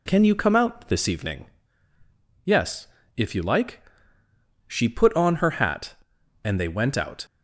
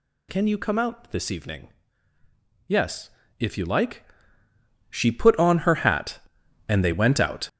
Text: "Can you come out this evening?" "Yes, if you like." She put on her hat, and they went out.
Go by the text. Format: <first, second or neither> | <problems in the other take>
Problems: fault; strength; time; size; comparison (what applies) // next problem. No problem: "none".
first | gets louder; strong; throughout; 9.5 dB